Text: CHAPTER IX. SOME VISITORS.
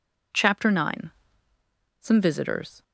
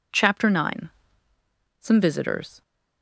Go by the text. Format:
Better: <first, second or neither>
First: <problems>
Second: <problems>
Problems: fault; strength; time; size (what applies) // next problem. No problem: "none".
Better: neither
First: none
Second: none